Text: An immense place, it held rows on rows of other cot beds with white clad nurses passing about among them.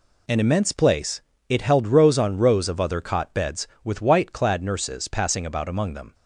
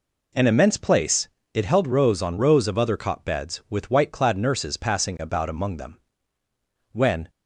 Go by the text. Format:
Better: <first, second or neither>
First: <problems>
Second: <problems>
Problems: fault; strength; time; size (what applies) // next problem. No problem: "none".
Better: first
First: none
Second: goes on to say "When"; slight; from 6.9 s on; 0.38 s long